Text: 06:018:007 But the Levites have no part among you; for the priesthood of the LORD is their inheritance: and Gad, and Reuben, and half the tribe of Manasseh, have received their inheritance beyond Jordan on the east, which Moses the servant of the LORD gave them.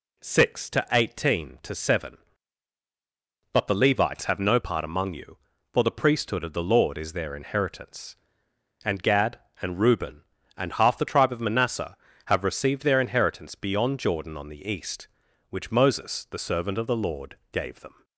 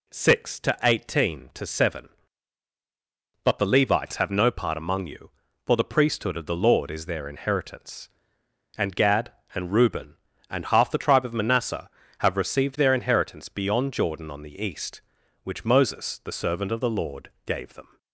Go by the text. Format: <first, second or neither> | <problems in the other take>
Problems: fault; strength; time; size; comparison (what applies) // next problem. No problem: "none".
neither | none